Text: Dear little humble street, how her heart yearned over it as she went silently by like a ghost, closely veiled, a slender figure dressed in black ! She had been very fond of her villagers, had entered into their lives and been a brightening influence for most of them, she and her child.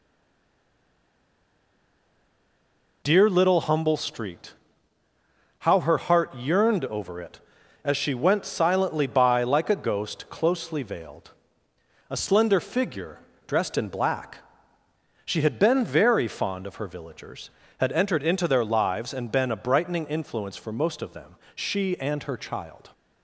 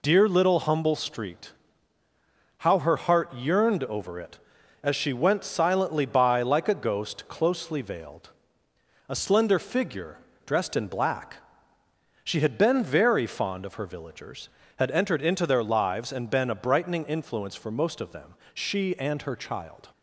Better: second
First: stays silent before the first word; strong; until 3.0 s; 3.0 s long // pauses between "figure" and "dressed"; slight; at 13.1 s; 0.30 s long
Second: pauses between "figure" and "dressed"; slight; at 10.1 s; 0.30 s long

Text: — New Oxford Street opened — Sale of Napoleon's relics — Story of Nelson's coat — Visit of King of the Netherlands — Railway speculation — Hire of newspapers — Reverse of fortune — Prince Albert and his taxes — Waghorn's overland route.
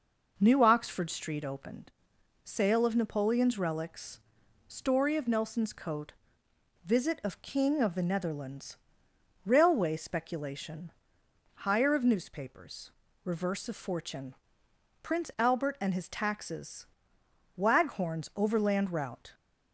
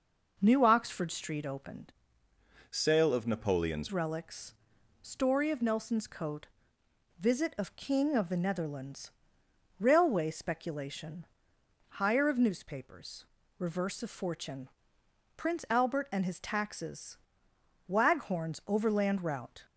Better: first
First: none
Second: changes voice from "Sale" to "Napoleon's"; from 2.7 to 3.8 s; 1.1 s long

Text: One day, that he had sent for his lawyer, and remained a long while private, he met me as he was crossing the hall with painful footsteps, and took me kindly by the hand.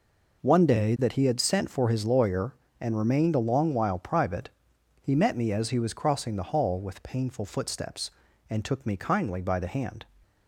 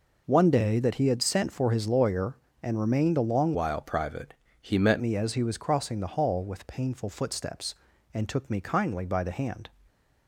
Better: first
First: none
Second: changes voice from "while" to "met"; from 3.5 to 4.9 s; 1.4 s long

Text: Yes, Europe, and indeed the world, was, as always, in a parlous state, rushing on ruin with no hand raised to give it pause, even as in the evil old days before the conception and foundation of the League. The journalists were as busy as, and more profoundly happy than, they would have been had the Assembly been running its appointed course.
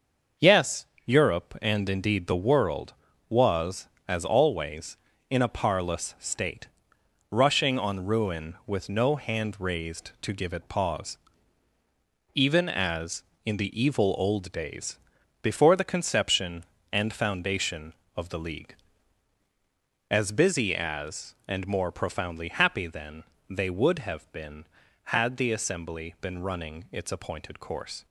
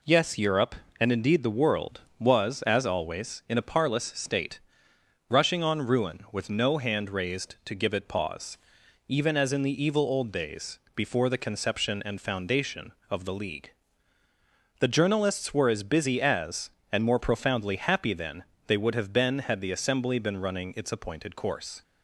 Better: second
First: starts louder than the rest; until 1.6 s; 6 dB // pauses between "days" and "before"; at 14.9 s; 0.44 s long // skips "The journalists were"; at 19.4 s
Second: pauses between "days" and "before"; slight; at 10.7 s; 0.18 s long

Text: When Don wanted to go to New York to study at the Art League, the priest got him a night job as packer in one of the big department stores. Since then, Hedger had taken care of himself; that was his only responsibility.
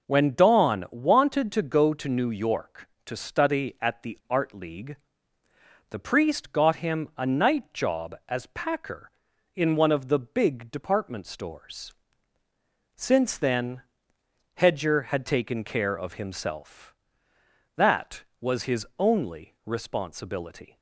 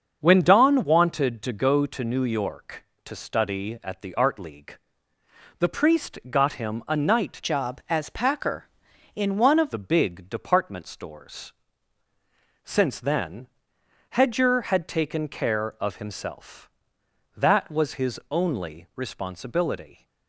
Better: first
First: none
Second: starts louder than the rest; until 1.2 s; 7 dB // changes voice from "job" to "of"; from 7.4 to 9.7 s; 2.3 s long

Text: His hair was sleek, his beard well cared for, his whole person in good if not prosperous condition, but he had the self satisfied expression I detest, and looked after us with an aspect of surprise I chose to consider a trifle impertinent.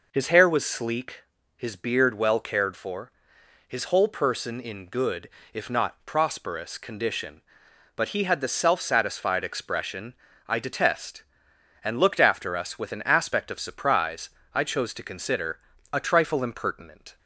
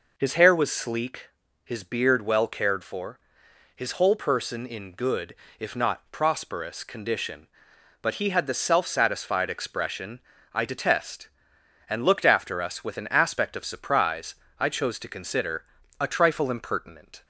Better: neither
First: pauses between "good" and "if"; slight; at 5.2 s; 0.24 s long // pauses between "expression" and "I"; slight; at 10.1 s; 0.34 s long // pauses between "surprise" and "I"; slight; at 14.2 s; 0.22 s long // pauses between "consider" and "a"; slight; at 15.5 s; 0.32 s long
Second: pauses between "good" and "if"; slight; at 5.3 s; 0.24 s long // pauses between "expression" and "I"; slight; at 10.1 s; 0.34 s long // pauses between "surprise" and "I"; slight; at 14.3 s; 0.22 s long // pauses between "consider" and "a"; slight; at 15.6 s; 0.34 s long

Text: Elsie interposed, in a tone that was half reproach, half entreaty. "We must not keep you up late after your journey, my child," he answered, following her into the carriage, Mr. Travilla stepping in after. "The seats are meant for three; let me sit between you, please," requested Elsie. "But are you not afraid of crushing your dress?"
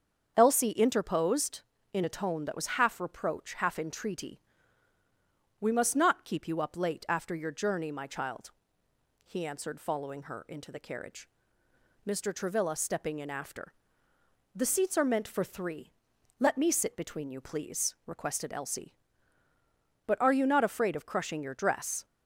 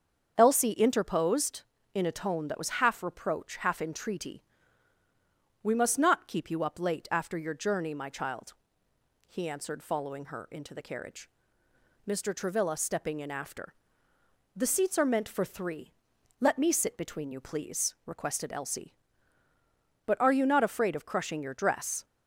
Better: neither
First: starts louder than the rest; strong; until 1.3 s; 7 dB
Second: starts louder than the rest; strong; until 1.3 s; 7 dB

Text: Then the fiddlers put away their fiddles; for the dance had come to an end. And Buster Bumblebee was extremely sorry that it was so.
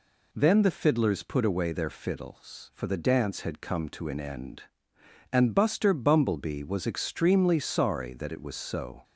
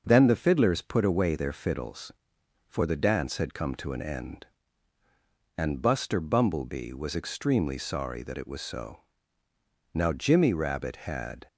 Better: first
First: none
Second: starts louder than the rest; noticeable; until 1.0 s; 6 dB // goes on to say "Now Jimmy Rabbit had"; from 9.9 s on; 1.5 s long

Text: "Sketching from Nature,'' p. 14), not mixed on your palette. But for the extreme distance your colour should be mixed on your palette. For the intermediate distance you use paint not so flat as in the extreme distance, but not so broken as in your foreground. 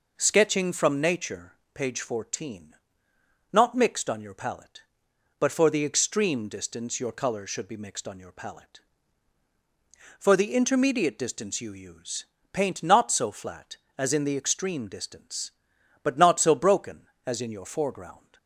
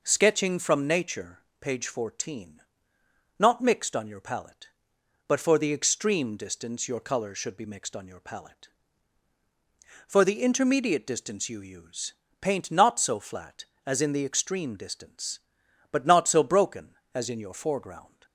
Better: neither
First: pauses between "use" and "paint"; slight; at 12.2 s; 0.28 s long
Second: pauses between "use" and "paint"; slight; at 12.1 s; 0.28 s long

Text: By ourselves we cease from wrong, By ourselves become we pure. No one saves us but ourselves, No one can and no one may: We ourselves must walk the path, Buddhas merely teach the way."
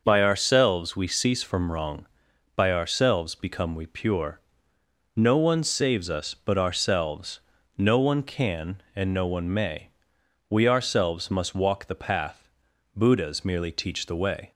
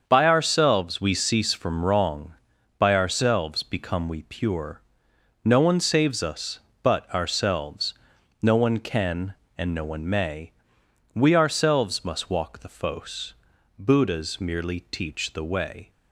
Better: first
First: starts louder than the rest; until 1.0 s; 6 dB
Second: starts louder than the rest; until 1.0 s; 7 dB // says "fos" for "path"; at 12.6 s

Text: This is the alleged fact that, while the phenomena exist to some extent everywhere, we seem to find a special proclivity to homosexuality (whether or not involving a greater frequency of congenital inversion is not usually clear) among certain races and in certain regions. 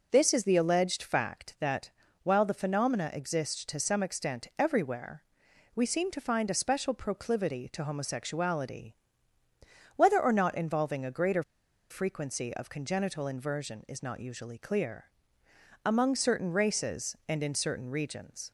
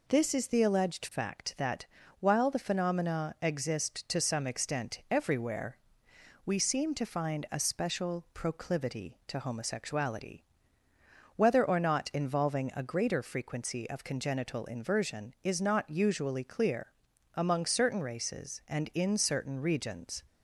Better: second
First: pauses between "greater" and "frequency"; noticeable; at 11.4 s; 0.48 s long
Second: none

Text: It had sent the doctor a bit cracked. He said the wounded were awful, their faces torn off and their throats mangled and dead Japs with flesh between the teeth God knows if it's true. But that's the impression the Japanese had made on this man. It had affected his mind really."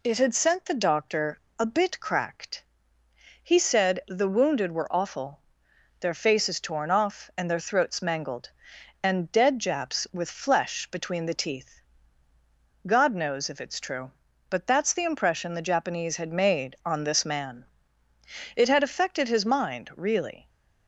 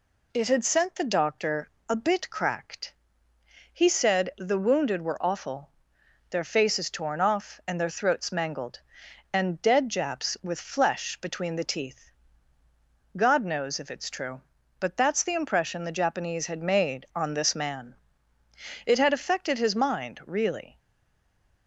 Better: first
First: pauses between "doctor" and "a"; slight; at 1.3 s; 0.20 s long // pauses between "teeth" and "God"; at 11.8 s; 1.0 s long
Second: pauses between "doctor" and "a"; slight; at 1.6 s; 0.20 s long // pauses between "teeth" and "God"; at 12.1 s; 1.0 s long // stays silent after the last word; slight; from 20.7 s on; 0.9 s long

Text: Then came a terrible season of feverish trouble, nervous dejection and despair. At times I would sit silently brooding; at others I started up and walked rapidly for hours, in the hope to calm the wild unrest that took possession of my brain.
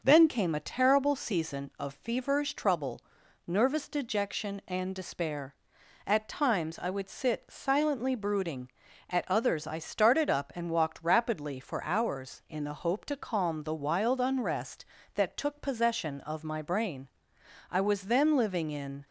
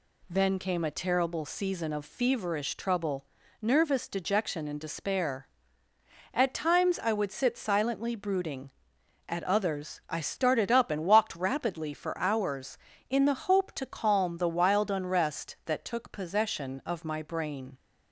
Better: second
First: goes on to say "I was then living in"; from 17.7 s on; 1.3 s long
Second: none

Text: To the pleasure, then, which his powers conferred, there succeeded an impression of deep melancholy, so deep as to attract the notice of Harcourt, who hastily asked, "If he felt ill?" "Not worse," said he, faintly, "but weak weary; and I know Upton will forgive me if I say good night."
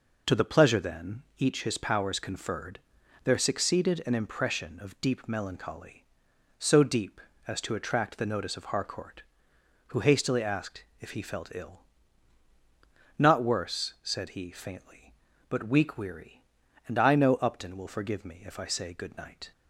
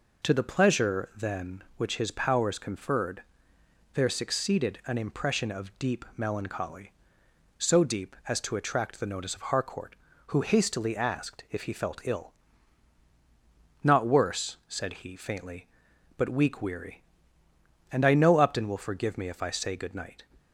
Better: second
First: says "each" for "which"; at 1.3 s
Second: none

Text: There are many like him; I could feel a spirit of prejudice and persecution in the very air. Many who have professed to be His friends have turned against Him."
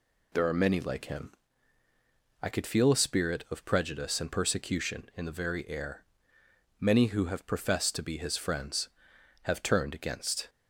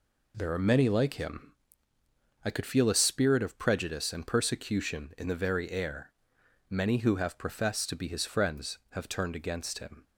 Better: second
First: stops before "Him"; at 10.4 s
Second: none

